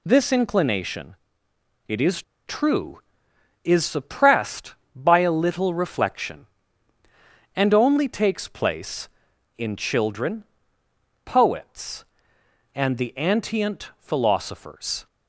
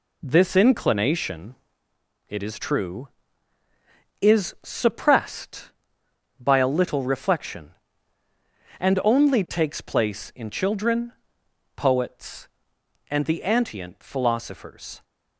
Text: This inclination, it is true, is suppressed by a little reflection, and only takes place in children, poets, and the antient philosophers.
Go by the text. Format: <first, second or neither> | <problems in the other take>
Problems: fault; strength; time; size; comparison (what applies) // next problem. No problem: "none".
second | pauses between "is" and "true"; slight; at 2.2 s; 0.25 s long